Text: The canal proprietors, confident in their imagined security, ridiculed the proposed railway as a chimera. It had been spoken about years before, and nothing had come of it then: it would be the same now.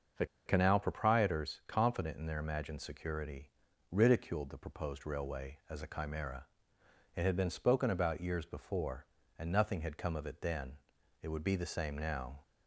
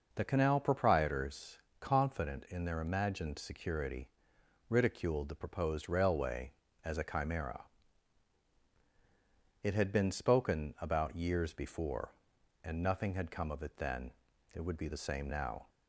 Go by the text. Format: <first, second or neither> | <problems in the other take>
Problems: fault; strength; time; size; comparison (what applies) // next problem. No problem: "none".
second | starts louder than the rest; until 1.3 s; 6 dB // pauses between "The" and "canal"; slight; at 0.2 s; 0.21 s long